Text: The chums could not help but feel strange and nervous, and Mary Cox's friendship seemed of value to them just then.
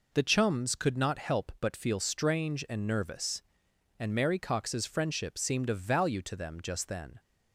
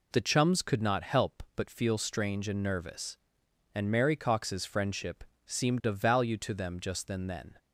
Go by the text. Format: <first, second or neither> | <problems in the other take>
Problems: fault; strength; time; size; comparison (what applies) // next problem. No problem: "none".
first | pauses between "friendship" and "seemed"; slight; at 5.2 s; 0.24 s long // says "then" twice; at 7.2 s